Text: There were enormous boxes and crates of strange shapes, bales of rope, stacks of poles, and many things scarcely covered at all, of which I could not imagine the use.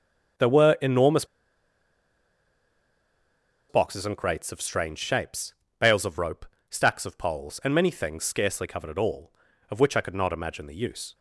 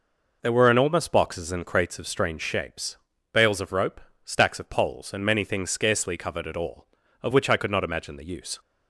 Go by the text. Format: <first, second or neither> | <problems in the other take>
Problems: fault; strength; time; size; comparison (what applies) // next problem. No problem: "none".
second | starts louder than the rest; strong; until 3.8 s; 7.5 dB // pauses between "enormous" and "boxes"; strong; at 1.2 s; 2.4 s long